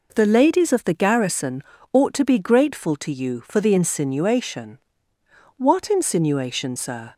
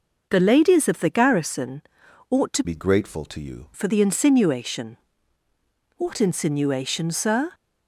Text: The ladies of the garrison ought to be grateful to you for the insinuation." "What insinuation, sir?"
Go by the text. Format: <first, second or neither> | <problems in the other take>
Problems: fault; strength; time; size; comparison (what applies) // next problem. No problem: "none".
first | pauses between "garrison" and "ought"; noticeable; at 1.8 s; 0.50 s long; slight in the first // changes voice from "be" to "you"; from 2.6 to 3.6 s; 1.0 s long